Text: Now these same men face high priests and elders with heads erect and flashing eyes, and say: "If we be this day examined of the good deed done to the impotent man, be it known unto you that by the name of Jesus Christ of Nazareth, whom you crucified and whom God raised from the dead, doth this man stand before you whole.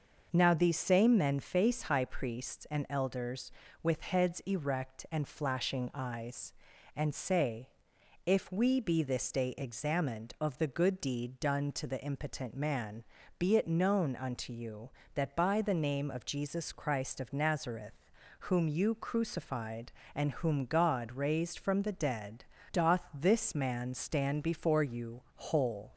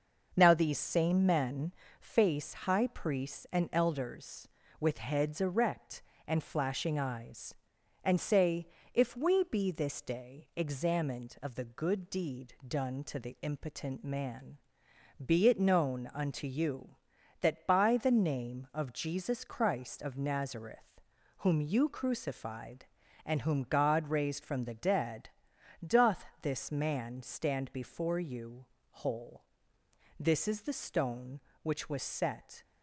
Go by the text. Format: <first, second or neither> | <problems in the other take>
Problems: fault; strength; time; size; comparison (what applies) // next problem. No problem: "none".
first | starts louder than the rest; noticeable; until 1.3 s; 6 dB; also in the first // pauses between "men" and "face"; slight; at 1.7 s; 0.28 s long // pauses between "doth" and "this"; slight; at 26.2 s; 0.16 s long // pauses between "you" and "whole"; slight; at 28.6 s; 0.26 s long // goes on to say "This is the stone which was set"; strong; from 30.1 s on; 2.4 s long